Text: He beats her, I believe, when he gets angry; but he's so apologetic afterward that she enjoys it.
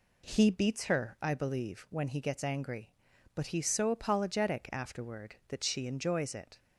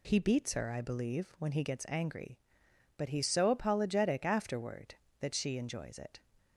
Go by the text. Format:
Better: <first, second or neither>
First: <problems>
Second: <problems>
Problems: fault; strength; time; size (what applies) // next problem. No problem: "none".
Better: neither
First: none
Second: none